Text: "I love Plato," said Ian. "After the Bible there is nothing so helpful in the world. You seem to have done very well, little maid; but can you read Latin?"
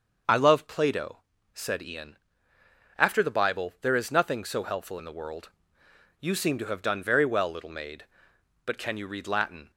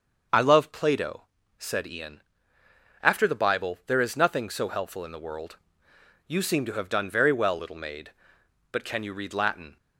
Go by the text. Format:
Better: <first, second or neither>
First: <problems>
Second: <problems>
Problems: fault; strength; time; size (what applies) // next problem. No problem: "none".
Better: neither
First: starts louder than the rest; until 1.5 s; 6.5 dB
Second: starts louder than the rest; until 1.6 s; 6.5 dB